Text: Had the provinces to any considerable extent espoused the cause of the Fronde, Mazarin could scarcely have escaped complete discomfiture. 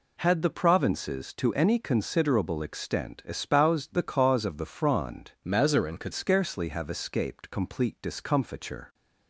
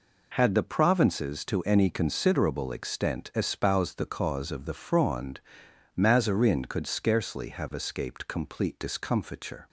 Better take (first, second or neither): second